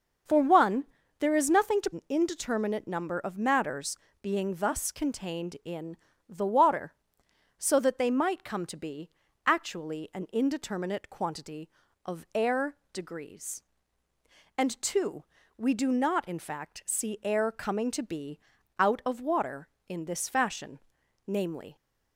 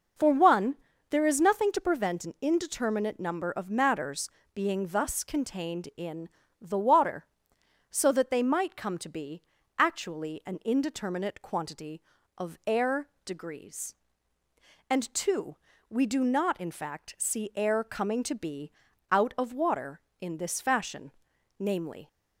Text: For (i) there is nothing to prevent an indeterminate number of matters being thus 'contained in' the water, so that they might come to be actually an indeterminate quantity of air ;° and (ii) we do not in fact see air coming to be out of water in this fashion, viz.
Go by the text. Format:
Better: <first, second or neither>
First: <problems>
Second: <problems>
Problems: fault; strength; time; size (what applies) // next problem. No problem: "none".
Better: second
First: starts louder than the rest; until 1.6 s; 6.5 dB // skips "prevent"; at 1.9 s // pauses between "matters" and "being"; slight; at 3.9 s; 0.24 s long // pauses between "in" and "the"; slight; at 5.9 s; 0.32 s long // pauses between "be" and "actually"; slight; at 9.0 s; 0.36 s long // pauses between "be" and "out"; at 18.3 s; 0.40 s long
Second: pauses between "matters" and "being"; slight; at 4.2 s; 0.24 s long // pauses between "in" and "the"; slight; at 6.2 s; 0.32 s long // pauses between "be" and "actually"; slight; at 9.4 s; 0.36 s long // pauses between "be" and "out"; at 18.6 s; 0.40 s long